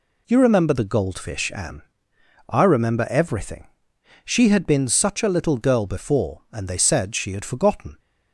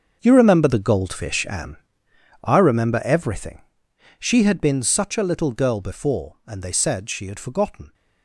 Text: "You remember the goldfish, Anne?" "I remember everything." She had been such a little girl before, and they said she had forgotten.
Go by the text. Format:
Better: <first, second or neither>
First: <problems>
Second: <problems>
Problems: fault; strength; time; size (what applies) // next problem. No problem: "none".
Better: first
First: none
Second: gets quieter; strong; throughout; 14 dB